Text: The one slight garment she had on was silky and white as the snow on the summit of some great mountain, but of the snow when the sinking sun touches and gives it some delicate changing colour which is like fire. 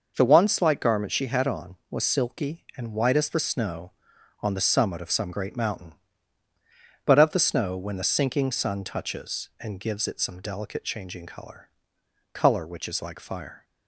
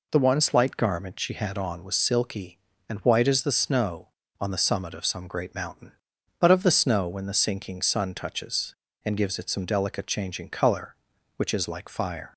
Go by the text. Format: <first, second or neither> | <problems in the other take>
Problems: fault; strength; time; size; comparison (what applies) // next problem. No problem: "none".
second | says "colour" twice; at 12.3 s